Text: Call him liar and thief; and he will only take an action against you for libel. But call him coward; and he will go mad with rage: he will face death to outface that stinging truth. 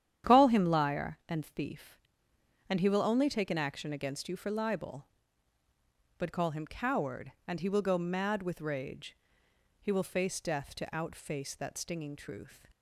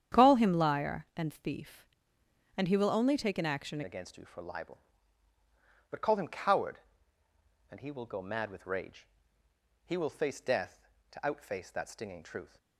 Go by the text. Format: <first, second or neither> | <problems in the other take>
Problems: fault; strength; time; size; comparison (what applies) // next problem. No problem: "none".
first | starts louder than the rest; strong; until 1.2 s; 9.5 dB; strong in the first // changes voice at "against"; from 3.8 s on; 8.7 s long